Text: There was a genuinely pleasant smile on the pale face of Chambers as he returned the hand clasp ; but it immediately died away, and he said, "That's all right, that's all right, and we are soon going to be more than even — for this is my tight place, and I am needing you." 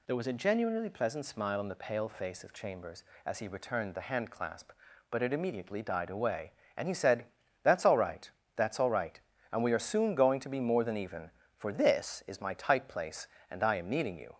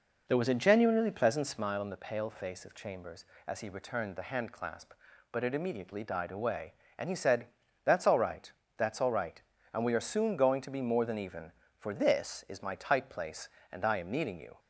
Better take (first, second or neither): first